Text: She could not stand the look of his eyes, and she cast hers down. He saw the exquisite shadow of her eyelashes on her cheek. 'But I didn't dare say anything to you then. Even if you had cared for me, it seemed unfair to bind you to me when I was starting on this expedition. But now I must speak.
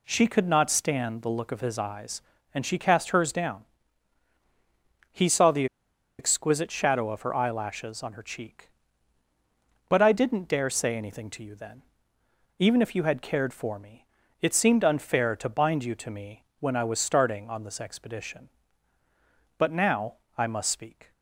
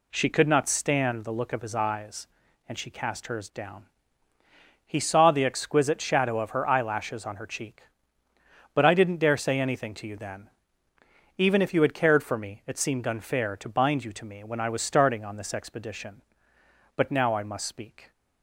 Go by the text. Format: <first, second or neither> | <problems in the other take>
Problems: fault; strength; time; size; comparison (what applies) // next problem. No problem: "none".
second | pauses between "the" and "exquisite"; noticeable; at 5.6 s; 0.53 s long // pauses between "me" and "when"; slight; at 16.4 s; 0.16 s long // pauses between "now" and "I"; slight; at 20.1 s; 0.24 s long